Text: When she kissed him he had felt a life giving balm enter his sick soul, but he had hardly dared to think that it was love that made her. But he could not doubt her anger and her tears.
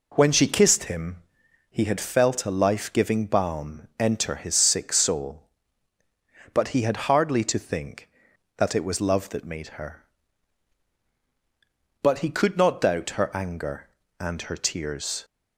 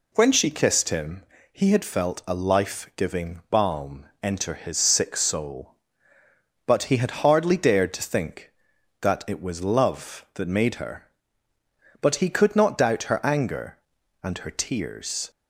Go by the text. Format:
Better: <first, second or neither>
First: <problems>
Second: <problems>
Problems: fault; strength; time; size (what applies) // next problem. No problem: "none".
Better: second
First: pauses between "him" and "he"; noticeable; at 1.1 s; 0.54 s long // skips "dared"; at 7.4 s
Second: pauses between "him" and "he"; slight; at 1.2 s; 0.30 s long